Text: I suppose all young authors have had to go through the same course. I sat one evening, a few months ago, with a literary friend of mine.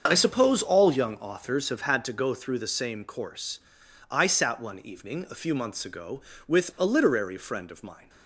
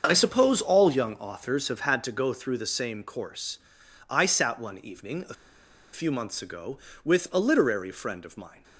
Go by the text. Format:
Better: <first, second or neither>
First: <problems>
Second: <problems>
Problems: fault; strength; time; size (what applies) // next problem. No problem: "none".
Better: first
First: starts louder than the rest; until 1.0 s; 6.5 dB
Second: starts louder than the rest; until 1.0 s; 6.5 dB // pauses between "a" and "few"; noticeable; at 5.3 s; 0.59 s long